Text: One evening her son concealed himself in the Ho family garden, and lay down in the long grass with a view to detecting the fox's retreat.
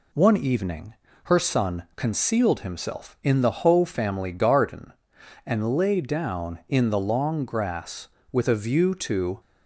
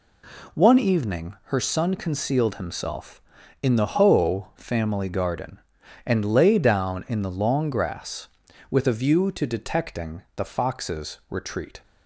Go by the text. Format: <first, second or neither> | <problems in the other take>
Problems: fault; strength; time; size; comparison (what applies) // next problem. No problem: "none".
second | pauses between "evening" and "her"; slight; at 0.9 s; 0.32 s long // stops before "detecting the fox's retreat"; at 9.3 s